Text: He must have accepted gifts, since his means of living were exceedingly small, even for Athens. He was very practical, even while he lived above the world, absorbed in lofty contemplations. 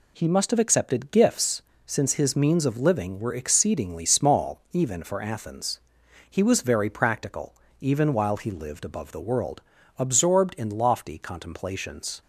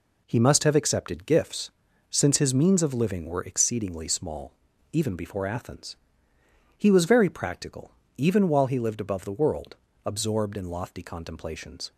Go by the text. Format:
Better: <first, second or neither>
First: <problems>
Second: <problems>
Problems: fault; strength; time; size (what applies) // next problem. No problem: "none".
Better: first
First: none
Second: says "before" for "for"; at 5.1 s